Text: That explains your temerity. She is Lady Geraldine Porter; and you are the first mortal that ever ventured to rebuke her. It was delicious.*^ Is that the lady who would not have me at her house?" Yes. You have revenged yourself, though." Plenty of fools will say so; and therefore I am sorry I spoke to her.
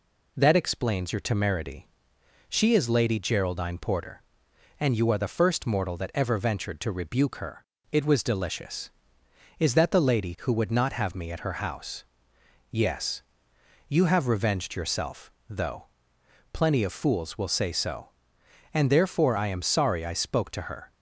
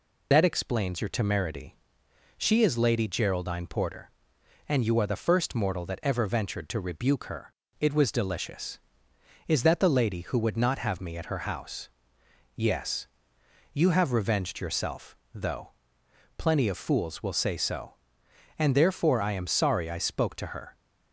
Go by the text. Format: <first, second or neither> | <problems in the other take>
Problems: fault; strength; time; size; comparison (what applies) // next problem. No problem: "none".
first | loses the start of "That"; at 0.3 s; 65 ms